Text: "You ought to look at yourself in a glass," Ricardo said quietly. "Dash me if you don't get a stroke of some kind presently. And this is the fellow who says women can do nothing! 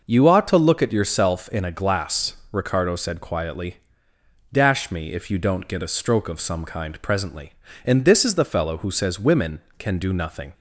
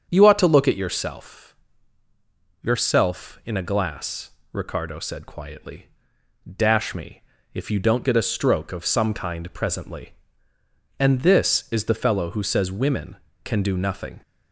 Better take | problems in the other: first | starts louder than the rest; strong; until 1.1 s; 7.5 dB // says "yourself" twice; at 2.6 s // pauses between "me" and "if"; slight; at 7.2 s; 0.30 s long

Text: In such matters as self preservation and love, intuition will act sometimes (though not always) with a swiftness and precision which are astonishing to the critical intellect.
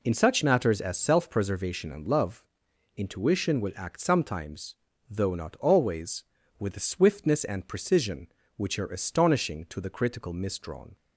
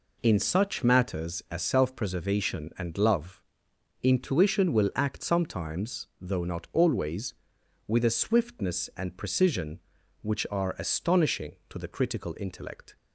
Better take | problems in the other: second | says "misdrawn" for "intellect"; at 10.3 s

